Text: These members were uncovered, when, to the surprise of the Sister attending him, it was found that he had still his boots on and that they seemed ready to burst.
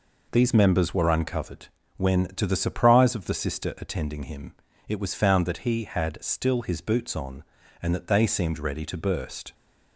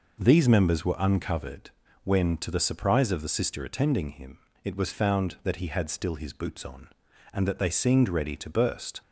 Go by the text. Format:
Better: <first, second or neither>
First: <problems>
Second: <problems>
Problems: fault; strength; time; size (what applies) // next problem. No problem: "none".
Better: neither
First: none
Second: none